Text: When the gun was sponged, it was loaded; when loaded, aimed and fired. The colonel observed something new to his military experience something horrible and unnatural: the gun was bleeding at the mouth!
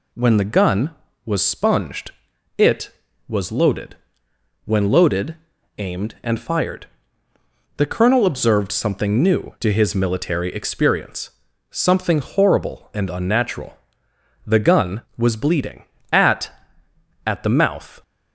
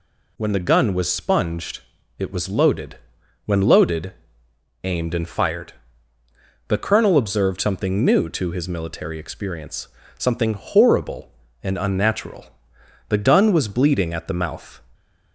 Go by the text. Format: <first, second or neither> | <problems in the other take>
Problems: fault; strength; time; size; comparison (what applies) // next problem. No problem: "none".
second | pauses between "experience" and "something"; at 11.3 s; 0.40 s long; slight in the second // says "at" twice; at 17.2 s